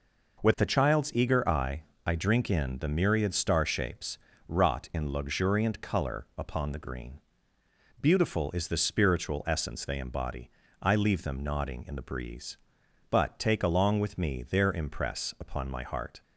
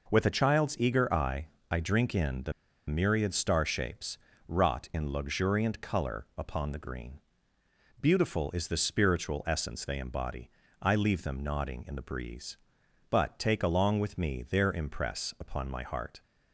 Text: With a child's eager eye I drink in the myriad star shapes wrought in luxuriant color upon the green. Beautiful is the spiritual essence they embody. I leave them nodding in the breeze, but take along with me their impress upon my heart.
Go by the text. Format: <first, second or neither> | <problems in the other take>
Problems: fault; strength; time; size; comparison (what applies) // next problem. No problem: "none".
first | pauses between "eye" and "I"; slight; at 1.4 s; 0.22 s long; slight in the first // pauses between "the" and "myriad"; slight; at 2.5 s; 0.35 s long // pauses between "shapes" and "wrought"; slight; at 4.1 s; 0.30 s long; slight in the first